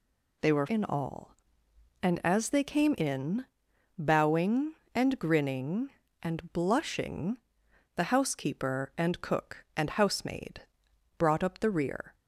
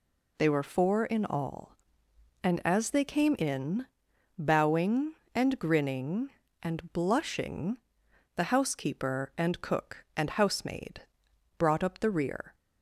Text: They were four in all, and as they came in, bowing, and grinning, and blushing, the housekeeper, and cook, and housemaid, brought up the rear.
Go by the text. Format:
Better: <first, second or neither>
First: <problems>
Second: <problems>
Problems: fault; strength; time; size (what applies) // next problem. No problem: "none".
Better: second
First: skips "four"; at 0.6 s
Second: none